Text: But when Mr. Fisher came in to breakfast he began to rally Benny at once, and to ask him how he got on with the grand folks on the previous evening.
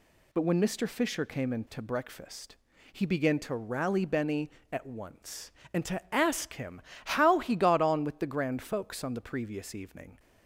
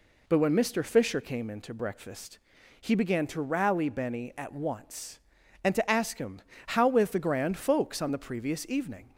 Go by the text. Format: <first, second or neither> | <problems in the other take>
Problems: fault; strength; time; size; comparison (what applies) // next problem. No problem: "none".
first | pauses between "breakfast" and "he"; at 2.3 s; 0.44 s long; also in the first // pauses between "him" and "how"; slight; at 6.3 s; 0.28 s long; slight in the first // skips "he got on"; at 6.8 s